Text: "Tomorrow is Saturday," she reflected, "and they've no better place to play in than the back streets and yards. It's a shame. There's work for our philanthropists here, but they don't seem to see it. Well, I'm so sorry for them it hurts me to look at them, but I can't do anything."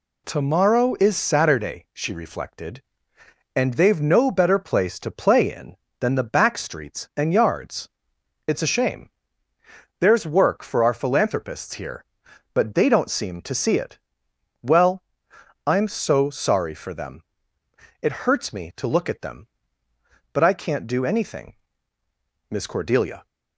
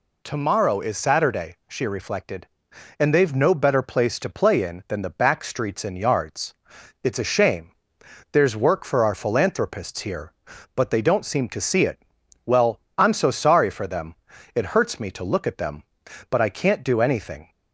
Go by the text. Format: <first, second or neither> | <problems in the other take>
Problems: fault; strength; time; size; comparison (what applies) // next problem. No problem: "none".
second | pauses between "them" and "it"; noticeable; at 17.2 s; 0.78 s long; also in the second // goes on to say "Miss Cordelia"; noticeable; from 22.4 s on; 0.76 s long